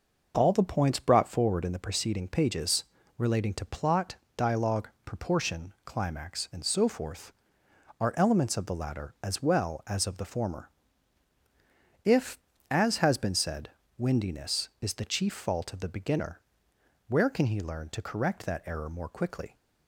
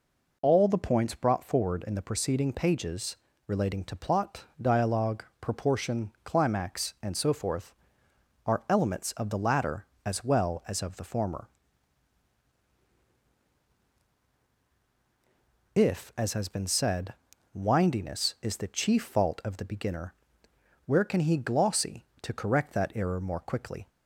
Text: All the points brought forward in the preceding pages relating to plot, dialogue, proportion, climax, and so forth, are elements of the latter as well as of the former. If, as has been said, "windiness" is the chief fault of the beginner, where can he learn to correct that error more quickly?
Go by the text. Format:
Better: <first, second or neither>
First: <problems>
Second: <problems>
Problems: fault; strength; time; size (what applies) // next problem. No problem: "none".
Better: first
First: pauses between "pages" and "relating"; slight; at 2.8 s; 0.32 s long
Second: pauses between "pages" and "relating"; slight; at 3.1 s; 0.30 s long // says "glossy" for "learn"; at 21.3 s